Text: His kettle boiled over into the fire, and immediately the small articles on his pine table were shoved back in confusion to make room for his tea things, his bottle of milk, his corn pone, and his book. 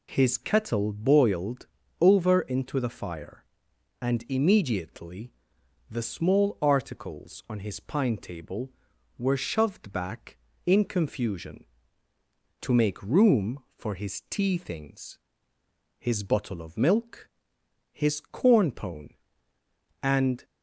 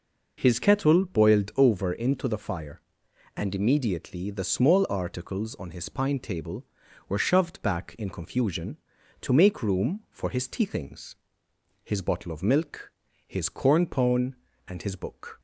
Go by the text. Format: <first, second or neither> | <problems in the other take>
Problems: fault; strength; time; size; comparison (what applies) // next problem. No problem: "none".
second | pauses between "boiled" and "over"; slight; at 1.6 s; 0.34 s long // pauses between "immediately" and "the"; noticeable; at 5.3 s; 0.58 s long // stops before "his book"; at 20.4 s